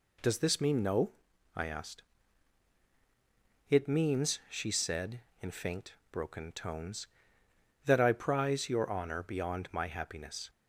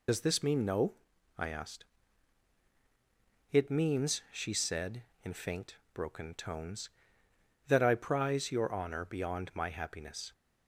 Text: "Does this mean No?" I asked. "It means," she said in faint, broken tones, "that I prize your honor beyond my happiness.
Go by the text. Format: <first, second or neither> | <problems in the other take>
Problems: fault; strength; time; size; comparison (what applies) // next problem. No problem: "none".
first | loses the start of "Does"; at 0.0 s; 75 ms